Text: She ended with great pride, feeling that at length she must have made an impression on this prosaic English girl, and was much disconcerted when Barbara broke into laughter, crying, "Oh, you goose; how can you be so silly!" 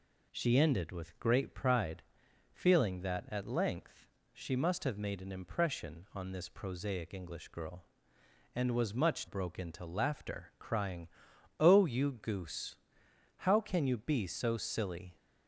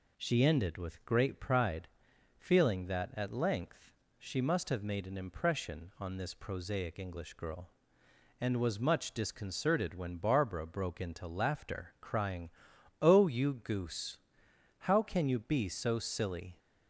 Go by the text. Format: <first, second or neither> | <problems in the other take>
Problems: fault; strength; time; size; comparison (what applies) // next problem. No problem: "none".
second | pauses between "length" and "she"; slight; at 4.0 s; 0.26 s long; slight in the second // skips "disconcerted when Barbara"; at 9.2 s